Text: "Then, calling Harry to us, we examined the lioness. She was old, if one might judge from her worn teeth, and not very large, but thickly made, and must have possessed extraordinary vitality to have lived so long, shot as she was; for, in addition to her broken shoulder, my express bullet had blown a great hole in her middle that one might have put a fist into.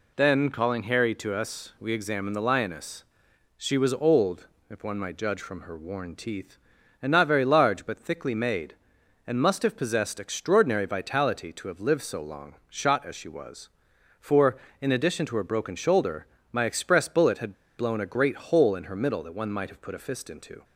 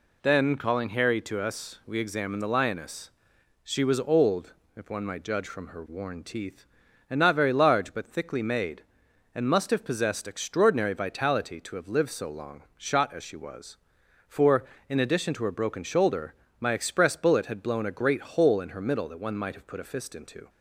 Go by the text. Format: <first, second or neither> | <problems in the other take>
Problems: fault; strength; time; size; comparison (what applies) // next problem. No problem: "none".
second | pauses between "had" and "blown"; slight; at 17.5 s; 0.22 s long